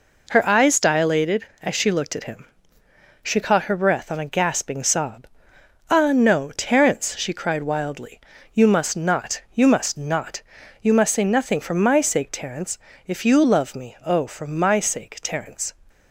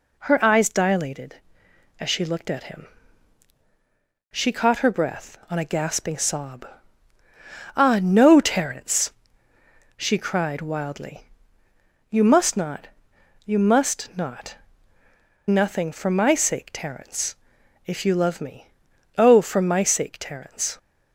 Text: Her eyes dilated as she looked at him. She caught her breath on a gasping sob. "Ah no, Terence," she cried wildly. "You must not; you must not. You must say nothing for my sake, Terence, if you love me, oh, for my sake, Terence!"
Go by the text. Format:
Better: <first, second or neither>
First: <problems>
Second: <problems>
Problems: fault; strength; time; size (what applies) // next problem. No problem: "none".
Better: first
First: none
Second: skips "You must say"; at 15.0 s